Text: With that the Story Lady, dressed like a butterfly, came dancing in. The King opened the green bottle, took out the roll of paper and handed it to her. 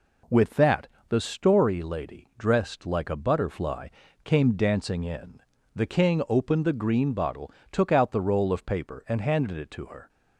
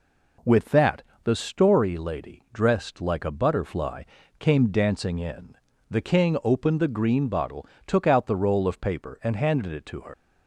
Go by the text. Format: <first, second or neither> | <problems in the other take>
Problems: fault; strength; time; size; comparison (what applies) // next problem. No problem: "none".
first | pauses between "that" and "the"; slight; at 1.0 s; 0.24 s long; slight in the first // leaves "her" unfinished; at 10.1 s; 95 ms